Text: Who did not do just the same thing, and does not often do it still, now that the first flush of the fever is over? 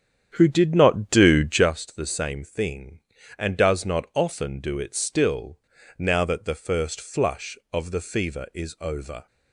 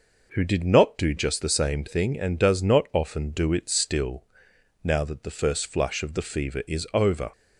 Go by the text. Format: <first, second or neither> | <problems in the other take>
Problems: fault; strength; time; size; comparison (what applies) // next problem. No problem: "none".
second | starts louder than the rest; strong; until 1.7 s; 9 dB